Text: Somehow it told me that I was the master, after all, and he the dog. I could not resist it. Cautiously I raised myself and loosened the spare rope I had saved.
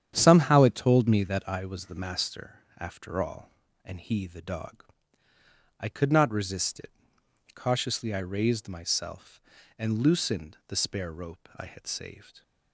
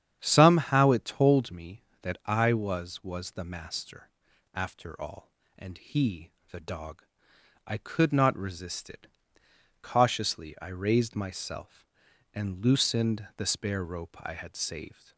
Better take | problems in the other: first | starts louder than the rest; strong; until 1.2 s; 9 dB; strong in the first // says "was" twice; at 3.0 s // pauses between "he" and "the"; slight; at 6.2 s; 0.22 s long

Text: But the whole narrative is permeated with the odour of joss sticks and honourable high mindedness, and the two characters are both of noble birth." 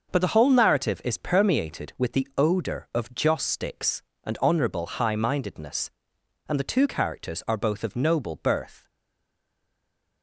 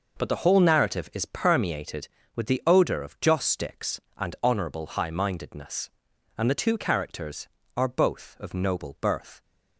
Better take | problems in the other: second | starts louder than the rest; noticeable; until 1.1 s; 6 dB // stays silent after the last word; noticeable; from 8.8 s on; 1.4 s long

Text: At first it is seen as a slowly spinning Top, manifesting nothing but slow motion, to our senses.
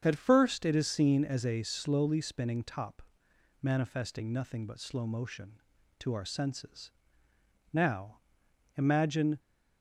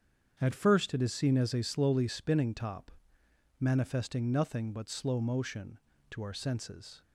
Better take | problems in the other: second | starts louder than the rest; strong; until 1.0 s; 7.5 dB; strong in the second // goes on to say "Now imagine"; from 7.7 s on; 1.6 s long

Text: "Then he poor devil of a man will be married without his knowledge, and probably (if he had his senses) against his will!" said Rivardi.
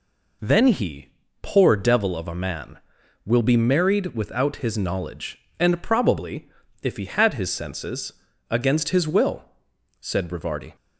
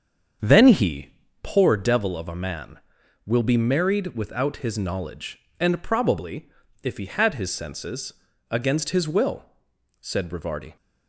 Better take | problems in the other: first | starts louder than the rest; strong; until 1.6 s; 7.5 dB // pauses between "he" and "poor"; slight; at 1.0 s; 0.32 s long; slight in the first

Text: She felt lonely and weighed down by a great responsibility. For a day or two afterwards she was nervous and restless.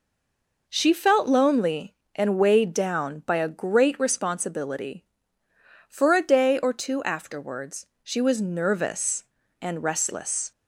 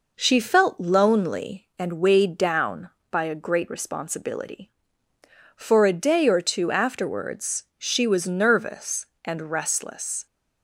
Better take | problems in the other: second | stays silent before the first word; slight; until 0.6 s; 0.6 s long // pauses between "afterwards" and "she"; slight; at 7.8 s; 0.18 s long

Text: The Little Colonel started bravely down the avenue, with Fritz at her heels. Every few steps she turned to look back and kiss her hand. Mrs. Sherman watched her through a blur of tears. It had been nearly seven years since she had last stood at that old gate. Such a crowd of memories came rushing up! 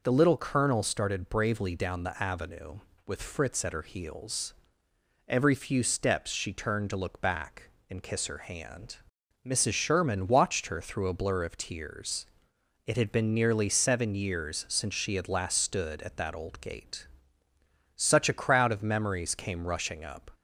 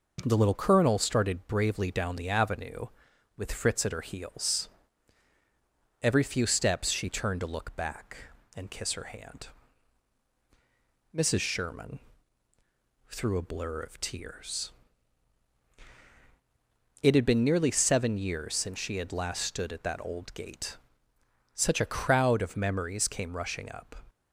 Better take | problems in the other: first | skips "watched her"; at 12.5 s

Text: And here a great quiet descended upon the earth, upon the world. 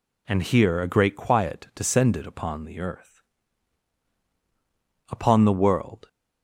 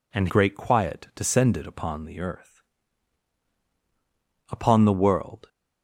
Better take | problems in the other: first | skips "here a"; at 0.2 s

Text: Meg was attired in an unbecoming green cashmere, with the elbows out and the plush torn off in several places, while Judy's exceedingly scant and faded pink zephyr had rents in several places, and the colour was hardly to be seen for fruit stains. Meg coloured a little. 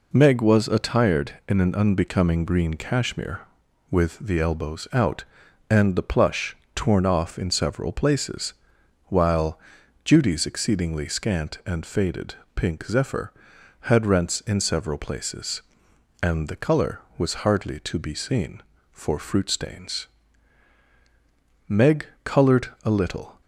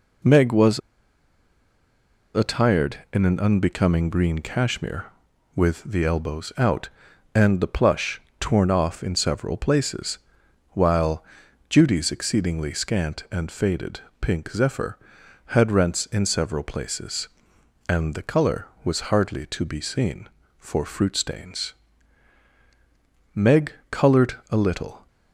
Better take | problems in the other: first | pauses between "was" and "attired"; strong; at 0.7 s; 1.5 s long // pauses between "plush" and "torn"; slight; at 8.1 s; 0.20 s long; slight in the first // pauses between "while" and "Judy's"; noticeable; at 11.2 s; 0.46 s long; noticeable in the first // pauses between "faded" and "pink"; slight; at 13.9 s; 0.22 s long; slight in the first // pauses between "Meg" and "coloured"; slight; at 23.7 s; 0.20 s long; slight in the first // pauses between "coloured" and "a"; slight; at 24.3 s; 0.16 s long; slight in the first

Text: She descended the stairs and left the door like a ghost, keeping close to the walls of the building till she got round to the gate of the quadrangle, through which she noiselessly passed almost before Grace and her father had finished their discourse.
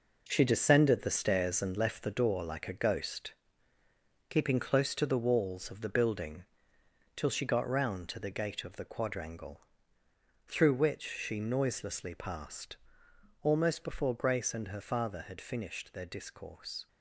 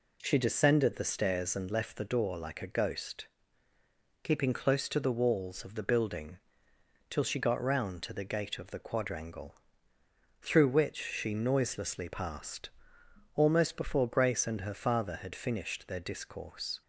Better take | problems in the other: second | gets quieter; strong; throughout; 9 dB // pauses between "building" and "till"; noticeable; at 6.4 s; 0.72 s long; noticeable in the second // pauses between "passed" and "almost"; noticeable; at 12.7 s; 0.66 s long; noticeable in the second

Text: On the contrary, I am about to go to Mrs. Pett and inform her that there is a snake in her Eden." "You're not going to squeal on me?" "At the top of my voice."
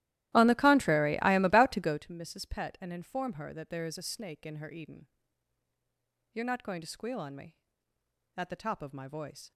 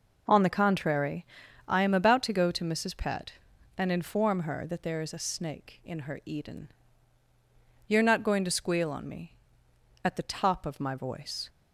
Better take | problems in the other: second | starts louder than the rest; strong; until 2.0 s; 15 dB

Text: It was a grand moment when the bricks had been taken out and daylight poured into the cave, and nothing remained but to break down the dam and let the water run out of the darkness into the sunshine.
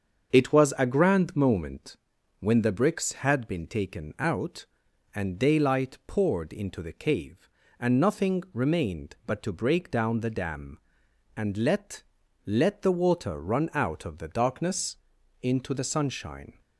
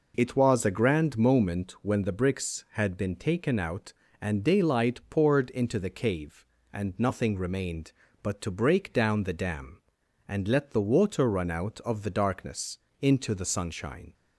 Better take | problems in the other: second | starts louder than the rest; until 1.3 s; 7 dB // pauses between "moment" and "when"; at 1.9 s; 0.42 s long // says "let" twice; at 12.4 s // pauses between "darkness" and "into"; noticeable; at 14.9 s; 0.46 s long; slight in the second

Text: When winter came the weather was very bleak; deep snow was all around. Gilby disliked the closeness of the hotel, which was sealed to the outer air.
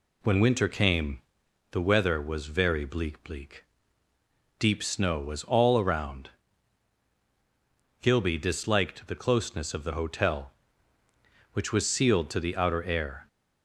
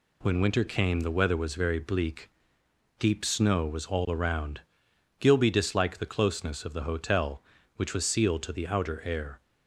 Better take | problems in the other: second | pauses between "came" and "the"; noticeable; at 1.2 s; 0.50 s long // says "bleak" twice; at 3.2 s

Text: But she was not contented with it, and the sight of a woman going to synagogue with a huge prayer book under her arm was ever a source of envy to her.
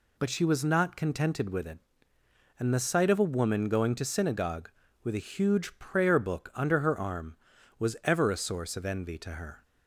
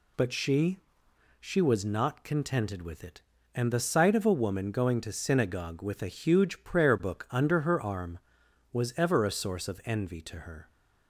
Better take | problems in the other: first | says "she" twice; at 1.3 s

